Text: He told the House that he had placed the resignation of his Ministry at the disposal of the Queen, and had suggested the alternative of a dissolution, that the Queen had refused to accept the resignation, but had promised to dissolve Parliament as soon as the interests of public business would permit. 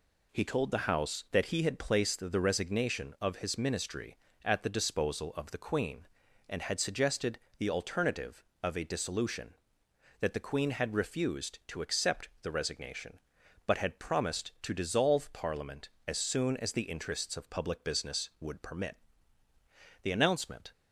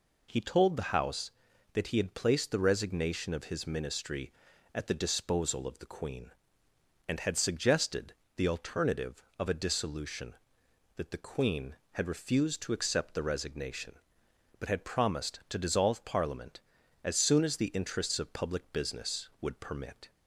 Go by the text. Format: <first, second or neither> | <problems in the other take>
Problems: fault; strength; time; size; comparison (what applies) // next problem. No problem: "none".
second | pauses between "suggested" and "the"; slight; at 7.3 s; 0.18 s long; slight in the second // goes on to say "The announcement"; noticeable; from 20.0 s on; 0.70 s long